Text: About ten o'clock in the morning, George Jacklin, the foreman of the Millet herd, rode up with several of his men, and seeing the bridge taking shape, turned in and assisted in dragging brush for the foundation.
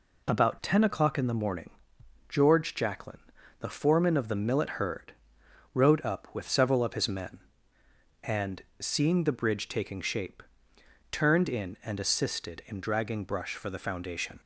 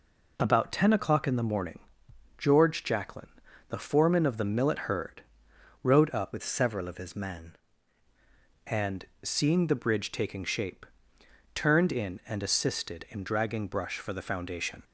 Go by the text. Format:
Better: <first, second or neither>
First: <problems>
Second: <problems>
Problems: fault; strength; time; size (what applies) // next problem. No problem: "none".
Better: first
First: pauses between "and" and "seeing"; slight; at 8.6 s; 0.18 s long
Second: changes voice from "with" to "men"; from 6.3 to 7.5 s; 1.2 s long // pauses between "and" and "seeing"; slight; at 9.0 s; 0.18 s long